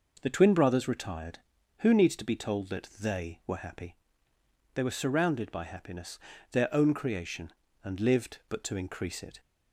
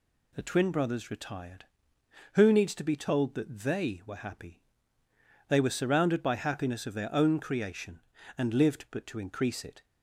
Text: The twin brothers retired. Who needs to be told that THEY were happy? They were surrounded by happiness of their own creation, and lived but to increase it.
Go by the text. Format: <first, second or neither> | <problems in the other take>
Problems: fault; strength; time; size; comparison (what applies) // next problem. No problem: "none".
second | skips "of"; at 6.3 s